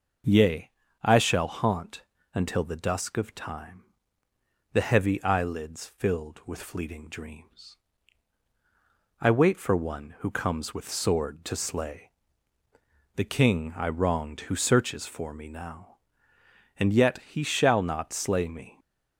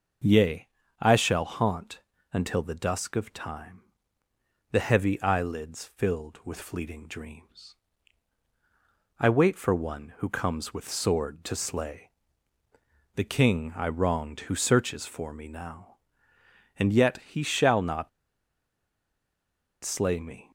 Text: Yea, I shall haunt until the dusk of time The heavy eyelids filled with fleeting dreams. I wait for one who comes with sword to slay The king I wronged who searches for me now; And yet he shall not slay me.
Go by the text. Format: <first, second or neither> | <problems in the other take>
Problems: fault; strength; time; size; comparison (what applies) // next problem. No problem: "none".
first | pauses between "haunt" and "until"; slight; at 1.9 s; 0.34 s long; slight in the first // pauses between "time" and "The"; noticeable; at 3.8 s; 0.90 s long; noticeable in the first // pauses between "slay" and "The"; at 12.1 s; 1.0 s long; also in the first // pauses between "not" and "slay"; strong; at 18.0 s; 1.7 s long